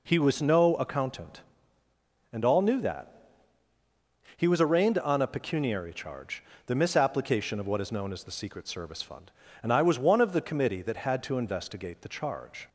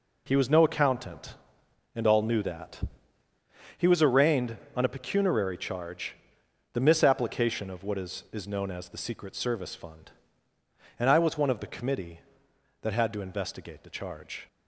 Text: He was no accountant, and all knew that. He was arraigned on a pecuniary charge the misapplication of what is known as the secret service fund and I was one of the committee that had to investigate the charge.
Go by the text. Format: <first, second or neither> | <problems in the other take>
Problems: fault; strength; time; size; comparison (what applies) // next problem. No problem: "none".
first | pauses between "charge" and "the"; noticeable; at 6.1 s; 0.58 s long; slight in the first // says "is" twice; at 8.3 s